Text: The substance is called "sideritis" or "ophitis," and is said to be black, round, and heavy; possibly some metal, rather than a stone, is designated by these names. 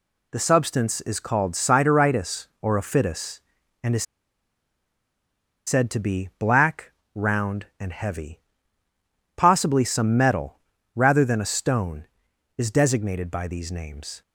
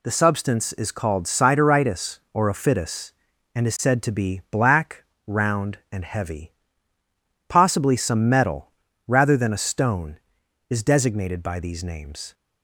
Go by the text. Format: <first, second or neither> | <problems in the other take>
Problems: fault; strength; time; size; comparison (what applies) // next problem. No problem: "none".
second | pauses between "is" and "said"; strong; at 4.0 s; 1.6 s long